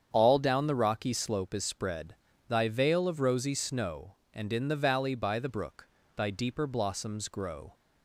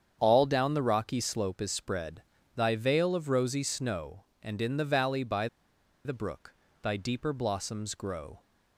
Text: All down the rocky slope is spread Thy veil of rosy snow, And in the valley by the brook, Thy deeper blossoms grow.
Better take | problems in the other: first | starts louder than the rest; strong; until 1.2 s; 8 dB; strong in the first // pauses between "spread" and "Thy"; slight; at 2.2 s; 0.34 s long; slight in the first // pauses between "by" and "the"; noticeable; at 5.4 s; 0.58 s long

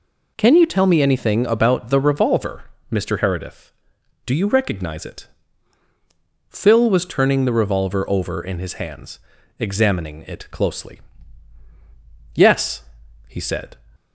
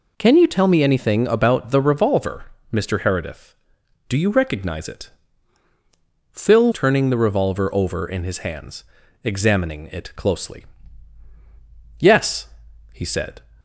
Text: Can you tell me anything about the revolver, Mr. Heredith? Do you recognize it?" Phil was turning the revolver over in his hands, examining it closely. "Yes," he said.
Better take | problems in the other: first | skips "was"; at 6.7 s

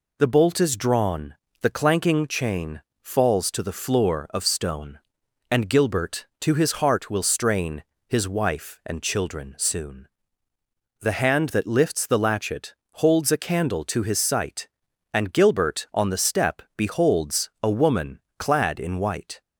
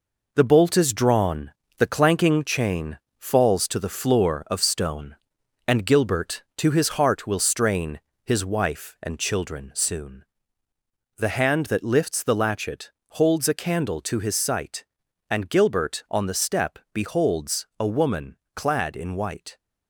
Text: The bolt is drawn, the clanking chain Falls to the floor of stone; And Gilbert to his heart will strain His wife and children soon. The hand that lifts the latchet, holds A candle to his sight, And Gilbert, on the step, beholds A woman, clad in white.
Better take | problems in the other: first | gets quieter; throughout; 7 dB // pauses between "chain" and "Falls"; slight; at 2.9 s; 0.20 s long; slight in the first // pauses between "strain" and "His"; slight; at 7.9 s; 0.24 s long; slight in the first

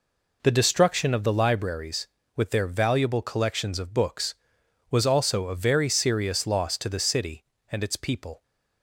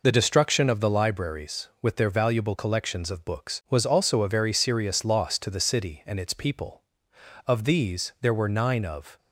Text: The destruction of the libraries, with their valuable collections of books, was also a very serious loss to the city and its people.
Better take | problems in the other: first | goes on to say "Of these there were nine of"; strong; from 7.4 s on; 1.7 s long

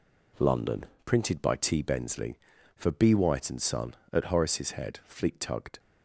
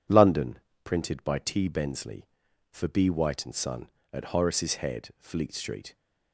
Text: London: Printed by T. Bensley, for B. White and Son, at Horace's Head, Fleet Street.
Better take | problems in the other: second | says "Tugged" for "Street"; at 5.3 s

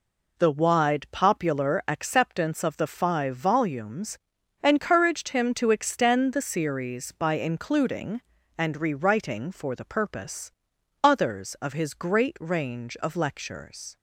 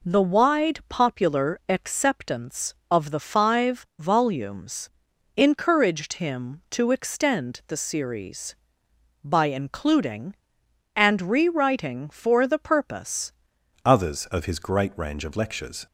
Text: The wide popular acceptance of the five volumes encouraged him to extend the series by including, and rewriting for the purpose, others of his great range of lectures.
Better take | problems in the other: first | pauses between "volumes" and "encouraged"; noticeable; at 4.8 s; 0.48 s long; also in the first // changes voice at "others"; from 13.8 s on; 2.0 s long

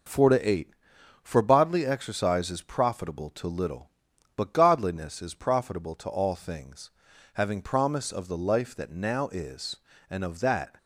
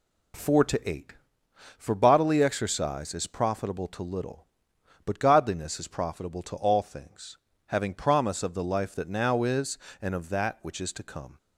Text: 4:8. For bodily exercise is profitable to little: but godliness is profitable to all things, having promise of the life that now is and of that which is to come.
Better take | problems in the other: second | stops before "which is to come"; at 10.7 s

